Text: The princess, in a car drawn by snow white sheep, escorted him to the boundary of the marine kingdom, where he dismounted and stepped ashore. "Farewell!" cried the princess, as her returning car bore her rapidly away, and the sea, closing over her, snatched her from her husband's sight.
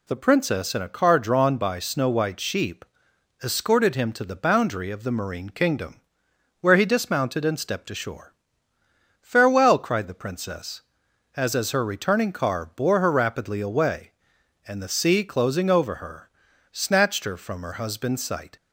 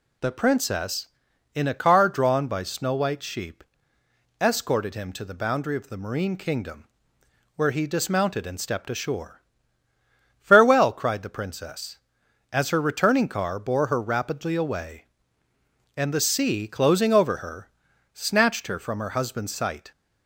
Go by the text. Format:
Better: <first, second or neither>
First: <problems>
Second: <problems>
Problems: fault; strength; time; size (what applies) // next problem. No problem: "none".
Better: second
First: says "as" twice; at 11.5 s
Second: none